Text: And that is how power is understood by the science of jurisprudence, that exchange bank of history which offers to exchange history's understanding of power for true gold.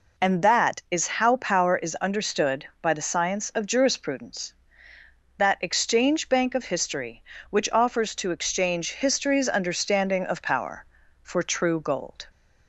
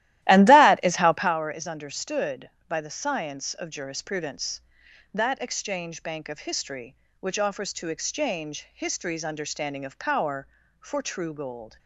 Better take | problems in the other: first | starts louder than the rest; strong; until 1.4 s; 14.5 dB

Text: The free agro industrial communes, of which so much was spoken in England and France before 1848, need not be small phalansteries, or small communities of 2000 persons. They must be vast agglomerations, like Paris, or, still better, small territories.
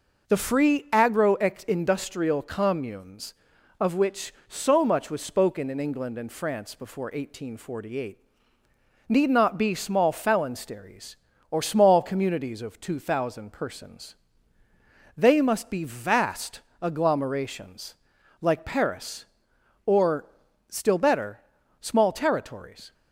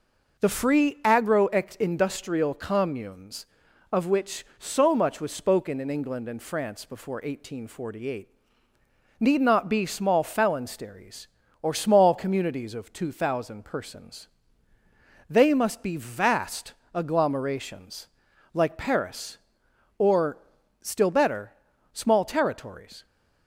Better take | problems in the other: neither | pauses between "vast" and "agglomerations"; slight; the same in both

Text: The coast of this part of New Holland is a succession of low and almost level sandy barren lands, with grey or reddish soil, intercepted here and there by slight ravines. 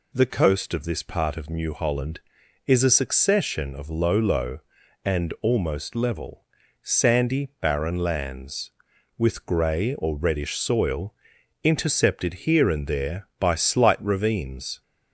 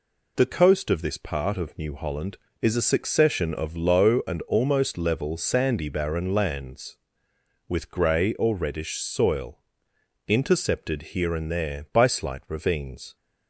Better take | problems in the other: second | says "low" twice; at 4.1 s // pauses between "level" and "sandy"; at 6.4 s; 0.38 s long

